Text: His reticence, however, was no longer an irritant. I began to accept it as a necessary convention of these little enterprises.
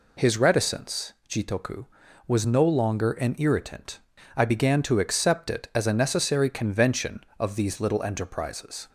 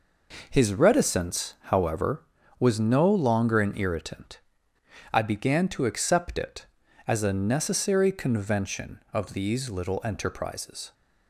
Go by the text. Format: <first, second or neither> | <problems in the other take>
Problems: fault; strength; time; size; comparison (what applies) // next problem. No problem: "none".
second | says "jitoku" for "however"; at 1.2 s